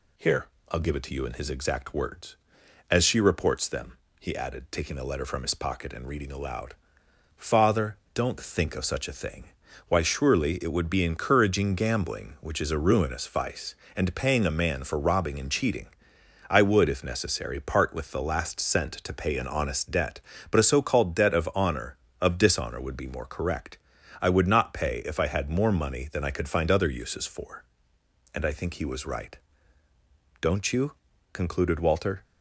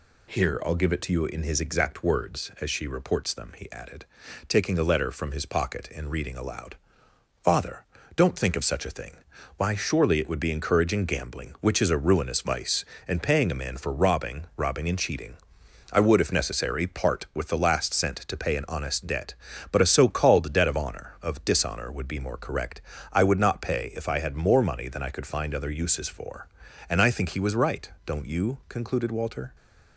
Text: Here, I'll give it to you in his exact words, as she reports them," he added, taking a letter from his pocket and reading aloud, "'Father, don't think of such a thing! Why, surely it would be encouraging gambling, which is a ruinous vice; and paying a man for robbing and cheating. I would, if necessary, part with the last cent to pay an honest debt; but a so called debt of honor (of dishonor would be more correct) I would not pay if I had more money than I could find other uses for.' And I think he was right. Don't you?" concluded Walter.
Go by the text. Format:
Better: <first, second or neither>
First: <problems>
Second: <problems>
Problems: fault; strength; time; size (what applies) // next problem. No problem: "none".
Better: first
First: none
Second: says "robbing" twice; at 14.5 s